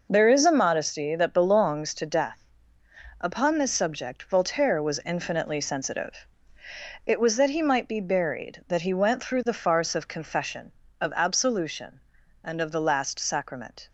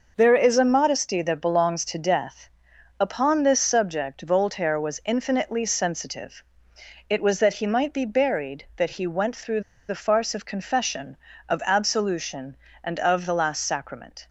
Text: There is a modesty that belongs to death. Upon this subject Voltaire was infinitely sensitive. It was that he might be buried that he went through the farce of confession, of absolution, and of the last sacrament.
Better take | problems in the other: first | pauses between "through" and "the"; slight; at 9.6 s; 0.26 s long

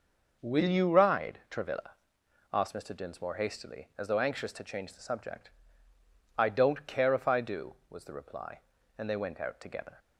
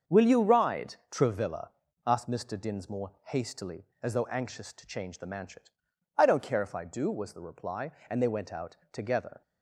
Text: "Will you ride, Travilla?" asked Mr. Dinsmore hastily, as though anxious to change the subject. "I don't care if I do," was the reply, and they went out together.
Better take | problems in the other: first | starts louder than the rest; until 1.2 s; 6.5 dB // says "manchet" for "subject"; at 5.2 s // pauses between "out" and "together"; slight; at 8.7 s; 0.16 s long

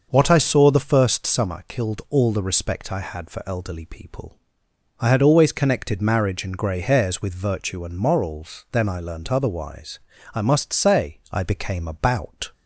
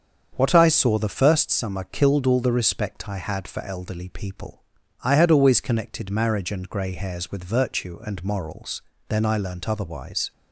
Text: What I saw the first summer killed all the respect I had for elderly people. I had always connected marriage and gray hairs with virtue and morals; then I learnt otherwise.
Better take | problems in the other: second | starts louder than the rest; until 1.1 s; 6 dB; strong in the second // goes on to say "I must say I became about"; strong; from 10.3 s on; 2.1 s long

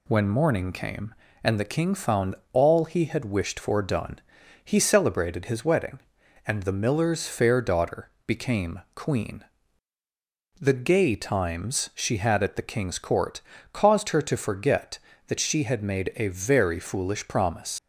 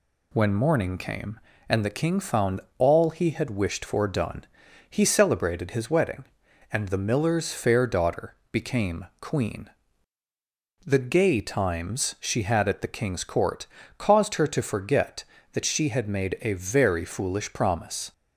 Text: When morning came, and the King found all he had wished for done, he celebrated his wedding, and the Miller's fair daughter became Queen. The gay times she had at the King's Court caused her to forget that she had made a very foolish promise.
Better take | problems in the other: second | pauses between "found" and "all"; slight; at 2.3 s; 0.16 s long; slight in the second // pauses between "daughter" and "became"; slight; at 8.0 s; 0.16 s long; slight in the second // pauses between "became" and "Queen"; slight; at 8.7 s; 0.16 s long; slight in the second // pauses between "Court" and "caused"; slight; at 13.4 s; 0.32 s long; slight in the second // leaves "promise" unfinished; at 17.7 s; 85 ms

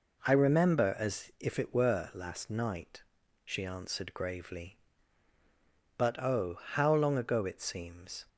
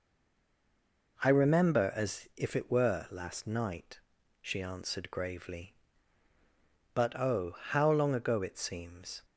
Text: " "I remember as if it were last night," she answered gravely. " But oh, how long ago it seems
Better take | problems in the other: first | stays silent before the first word; noticeable; until 1.1 s; 1.1 s long

